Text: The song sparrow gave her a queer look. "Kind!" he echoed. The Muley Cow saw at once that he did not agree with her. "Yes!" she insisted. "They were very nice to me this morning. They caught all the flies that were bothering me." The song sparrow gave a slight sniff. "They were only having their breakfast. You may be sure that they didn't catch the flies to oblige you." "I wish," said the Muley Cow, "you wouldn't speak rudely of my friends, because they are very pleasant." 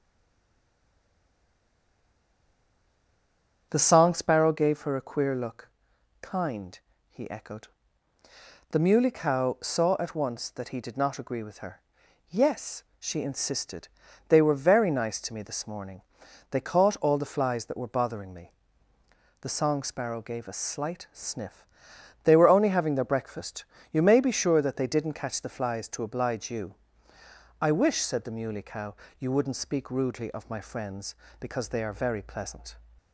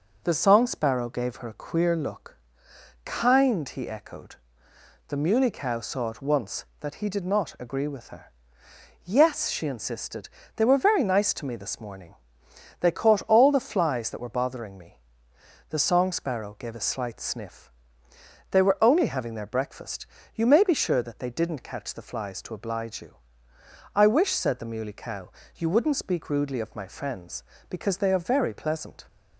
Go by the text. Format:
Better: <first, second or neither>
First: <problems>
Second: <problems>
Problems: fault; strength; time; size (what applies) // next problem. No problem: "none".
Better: second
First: stays silent before the first word; strong; until 3.6 s; 3.6 s long // starts louder than the rest; noticeable; until 4.7 s; 6 dB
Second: none